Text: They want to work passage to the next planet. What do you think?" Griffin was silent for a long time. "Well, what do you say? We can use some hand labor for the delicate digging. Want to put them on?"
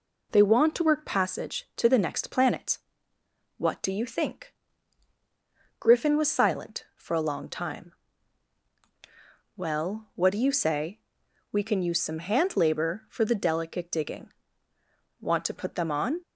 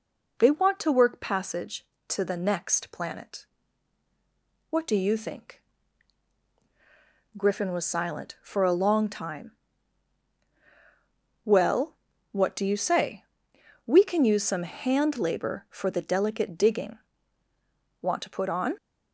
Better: first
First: none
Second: skips "them"; at 18.4 s

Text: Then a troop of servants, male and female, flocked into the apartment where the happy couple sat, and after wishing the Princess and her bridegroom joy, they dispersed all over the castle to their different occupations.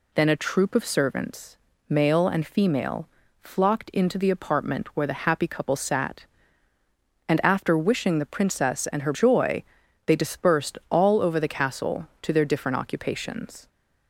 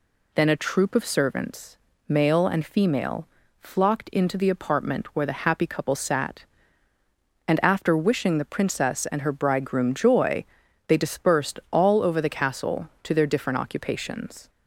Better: second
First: skips "bridegroom"; at 9.1 s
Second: none

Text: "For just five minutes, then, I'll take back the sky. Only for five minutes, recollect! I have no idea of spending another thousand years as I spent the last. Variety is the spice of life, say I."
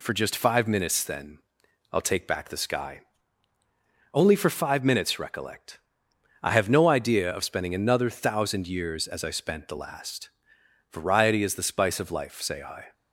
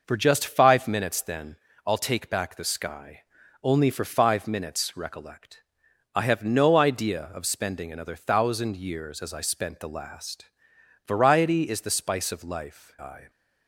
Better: first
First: none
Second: skips "say"; at 12.9 s

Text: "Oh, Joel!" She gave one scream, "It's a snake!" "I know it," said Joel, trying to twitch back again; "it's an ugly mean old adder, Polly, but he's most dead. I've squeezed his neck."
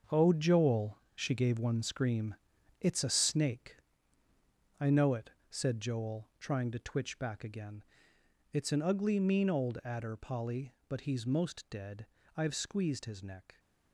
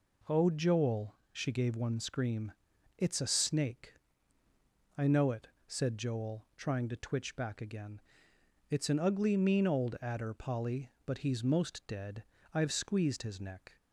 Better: second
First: gets quieter; strong; throughout; 9 dB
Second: none

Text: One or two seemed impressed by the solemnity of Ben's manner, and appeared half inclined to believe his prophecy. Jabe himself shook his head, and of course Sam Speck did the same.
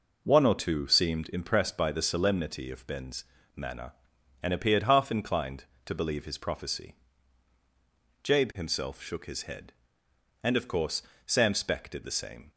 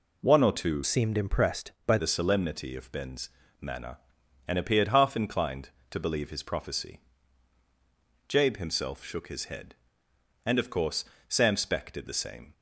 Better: first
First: pauses between "Ben's" and "manner"; slight; at 3.2 s; 0.30 s long // pauses between "course" and "Sam"; slight; at 11.0 s; 0.26 s long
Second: changes voice from "seemed" to "by"; from 0.8 to 1.9 s; 1.1 s long // pauses between "Ben's" and "manner"; slight; at 3.3 s; 0.30 s long // pauses between "course" and "Sam"; slight; at 11.0 s; 0.26 s long

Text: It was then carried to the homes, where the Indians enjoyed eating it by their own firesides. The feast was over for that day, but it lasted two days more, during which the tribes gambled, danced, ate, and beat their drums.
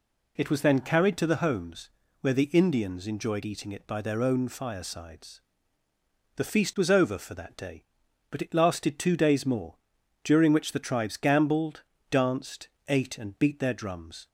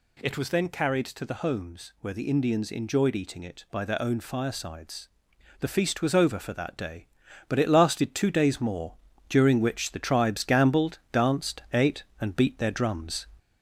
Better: first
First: none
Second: gets louder; slight; throughout; 3 dB

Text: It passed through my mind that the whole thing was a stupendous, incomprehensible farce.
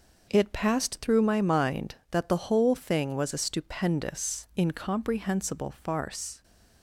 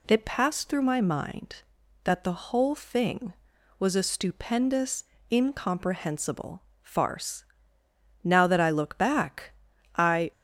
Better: first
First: none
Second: pauses between "incomprehensible" and "farce"; slight; at 6.6 s; 0.22 s long // goes on to say "Now that I look back I"; strong; from 8.2 s on; 2.0 s long

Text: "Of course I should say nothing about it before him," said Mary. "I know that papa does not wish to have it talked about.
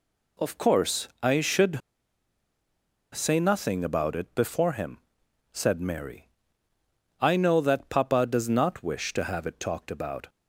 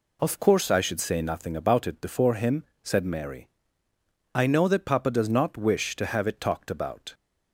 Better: second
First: pauses between "course" and "I"; slight; at 1.0 s; 0.16 s long // pauses between "should" and "say"; strong; at 1.8 s; 1.3 s long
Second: none

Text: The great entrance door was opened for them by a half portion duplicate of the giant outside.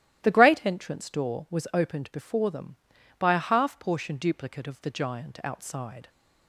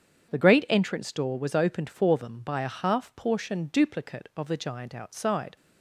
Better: second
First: starts louder than the rest; strong; until 1.2 s; 13.5 dB // says "before" for "for"; at 2.1 s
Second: starts louder than the rest; strong; until 1.3 s; 8 dB

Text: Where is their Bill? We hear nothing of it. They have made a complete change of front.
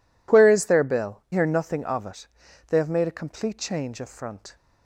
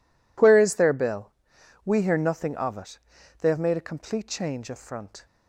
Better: second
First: skips "We"; at 1.2 s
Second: none

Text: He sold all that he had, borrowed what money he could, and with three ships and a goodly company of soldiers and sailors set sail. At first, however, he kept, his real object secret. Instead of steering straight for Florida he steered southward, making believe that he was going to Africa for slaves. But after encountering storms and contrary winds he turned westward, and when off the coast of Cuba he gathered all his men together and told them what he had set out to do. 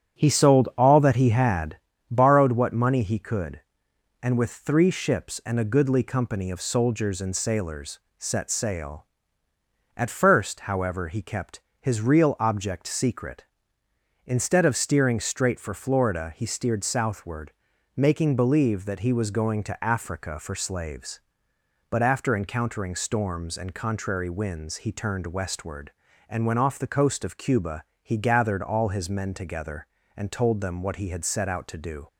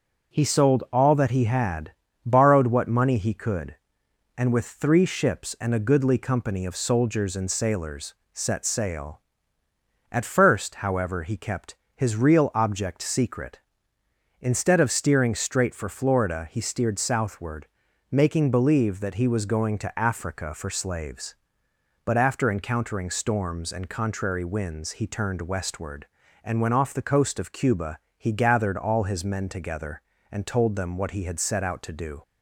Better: second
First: starts louder than the rest; strong; until 1.9 s; 8.5 dB // pauses between "sailors" and "set"; slight; at 7.9 s; 0.18 s long // pauses between "Cuba" and "he"; slight; at 27.8 s; 0.18 s long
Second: pauses between "sailors" and "set"; slight; at 8.1 s; 0.18 s long // pauses between "Cuba" and "he"; slight; at 27.9 s; 0.18 s long

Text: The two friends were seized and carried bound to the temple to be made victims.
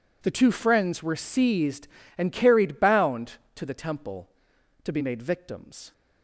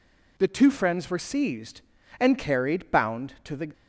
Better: first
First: none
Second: stops before "temple to be made victims"; at 3.7 s

